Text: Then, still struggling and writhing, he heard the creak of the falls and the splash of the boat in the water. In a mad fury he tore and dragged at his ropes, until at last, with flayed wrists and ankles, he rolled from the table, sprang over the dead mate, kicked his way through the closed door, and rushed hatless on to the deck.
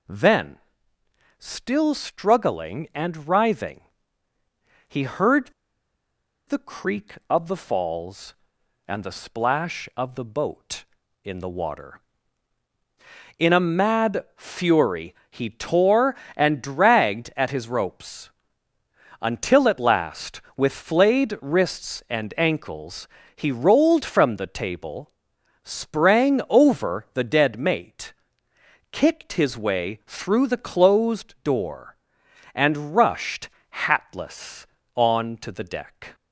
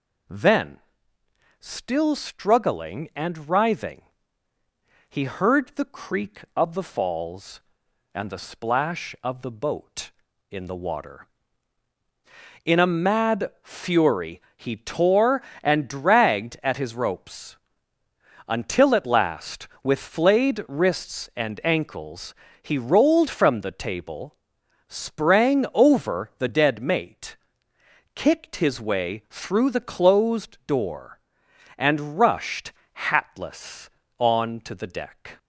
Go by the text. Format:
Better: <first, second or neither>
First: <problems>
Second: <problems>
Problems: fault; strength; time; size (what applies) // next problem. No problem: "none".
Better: second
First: pauses between "heard" and "the"; at 5.5 s; 0.98 s long // pauses between "fury" and "he"; slight; at 15.1 s; 0.16 s long // pauses between "rushed" and "hatless"; slight; at 33.4 s; 0.22 s long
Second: pauses between "fury" and "he"; slight; at 14.4 s; 0.16 s long // pauses between "rushed" and "hatless"; slight; at 32.7 s; 0.22 s long